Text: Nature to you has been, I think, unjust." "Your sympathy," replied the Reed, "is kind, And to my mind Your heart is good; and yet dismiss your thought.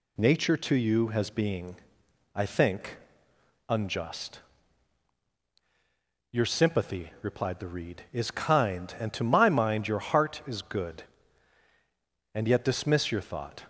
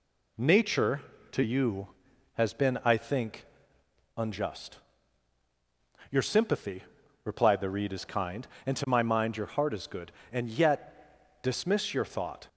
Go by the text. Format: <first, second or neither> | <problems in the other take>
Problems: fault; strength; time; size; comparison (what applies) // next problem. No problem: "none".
second | says "being" for "been"; at 1.2 s